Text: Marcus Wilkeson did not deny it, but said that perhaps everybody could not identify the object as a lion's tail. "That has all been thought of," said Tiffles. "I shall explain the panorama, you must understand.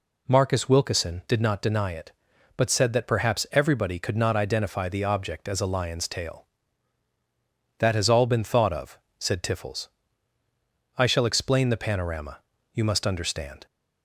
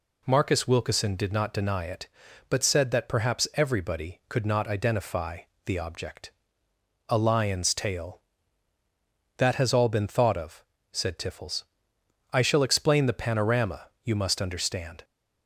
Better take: first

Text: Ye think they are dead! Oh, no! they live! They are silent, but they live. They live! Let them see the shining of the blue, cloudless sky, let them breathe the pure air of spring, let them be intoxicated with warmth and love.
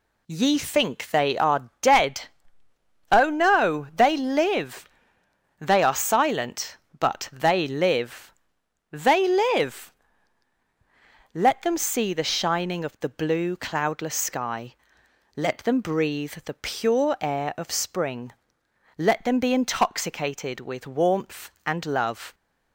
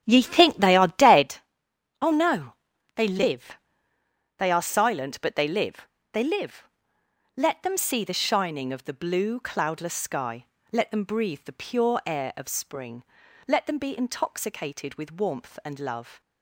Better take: first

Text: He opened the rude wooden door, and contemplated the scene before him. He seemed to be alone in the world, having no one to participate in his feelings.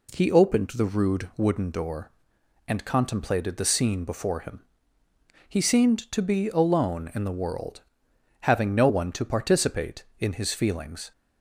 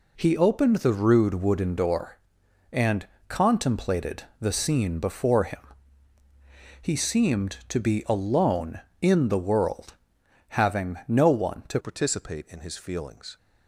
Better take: first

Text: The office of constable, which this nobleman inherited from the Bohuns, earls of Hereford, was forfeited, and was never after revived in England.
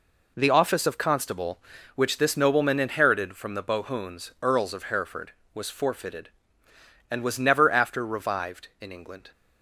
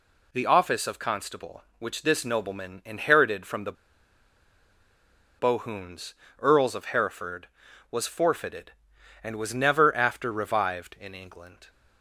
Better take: first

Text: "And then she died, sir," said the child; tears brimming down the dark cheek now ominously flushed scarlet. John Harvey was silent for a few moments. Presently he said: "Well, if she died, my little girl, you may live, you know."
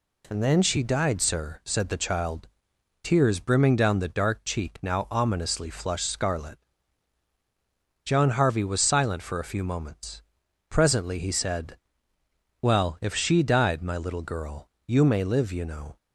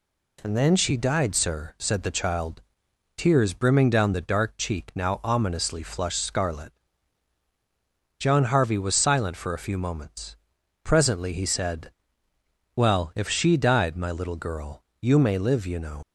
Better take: first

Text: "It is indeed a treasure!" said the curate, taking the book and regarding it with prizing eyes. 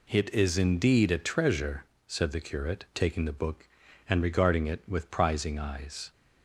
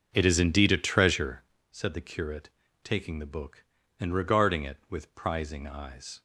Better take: first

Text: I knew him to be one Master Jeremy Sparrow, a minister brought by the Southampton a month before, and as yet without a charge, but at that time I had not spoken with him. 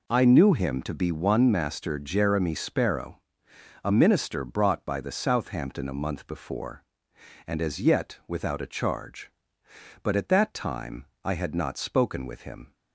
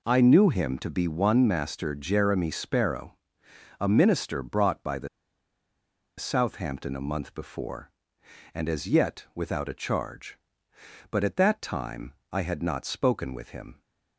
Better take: first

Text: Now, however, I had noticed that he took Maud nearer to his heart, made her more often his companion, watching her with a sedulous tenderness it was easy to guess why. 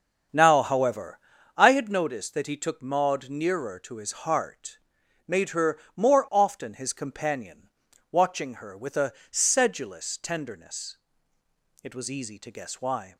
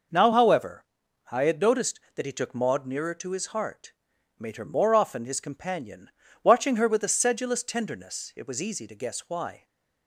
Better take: second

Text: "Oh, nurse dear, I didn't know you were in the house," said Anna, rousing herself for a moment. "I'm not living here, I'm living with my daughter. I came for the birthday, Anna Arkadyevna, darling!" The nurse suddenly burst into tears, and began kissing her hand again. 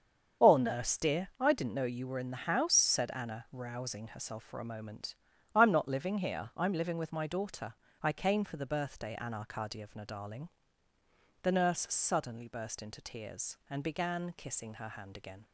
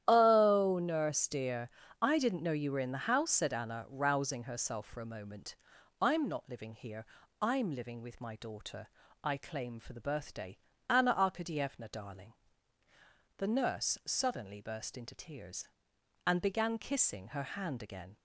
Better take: first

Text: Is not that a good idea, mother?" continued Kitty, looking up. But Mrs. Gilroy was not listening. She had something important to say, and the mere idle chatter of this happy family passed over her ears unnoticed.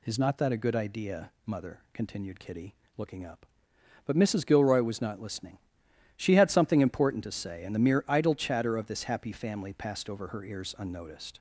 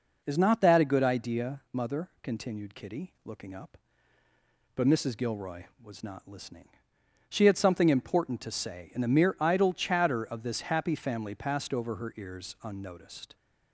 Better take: neither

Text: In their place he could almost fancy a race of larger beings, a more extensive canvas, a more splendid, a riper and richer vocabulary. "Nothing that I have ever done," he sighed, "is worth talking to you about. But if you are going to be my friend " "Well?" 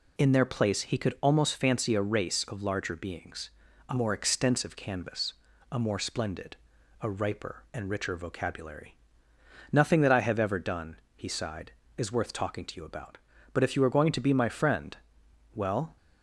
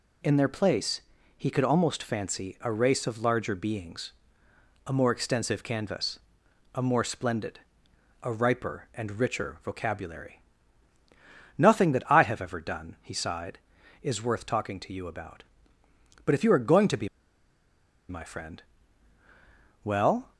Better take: first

